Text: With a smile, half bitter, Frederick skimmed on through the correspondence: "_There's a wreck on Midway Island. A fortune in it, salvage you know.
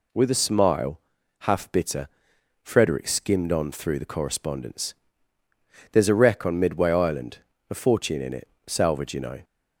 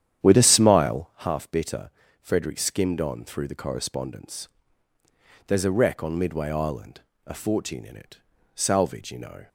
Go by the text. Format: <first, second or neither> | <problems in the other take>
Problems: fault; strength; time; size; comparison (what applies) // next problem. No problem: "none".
first | starts louder than the rest; strong; until 1.3 s; 10 dB